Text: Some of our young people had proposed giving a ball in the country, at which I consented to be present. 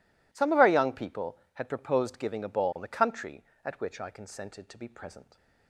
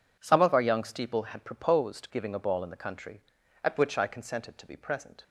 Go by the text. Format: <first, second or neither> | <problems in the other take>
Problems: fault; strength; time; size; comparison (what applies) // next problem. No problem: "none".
first | says "steeple" for "people"; at 0.8 s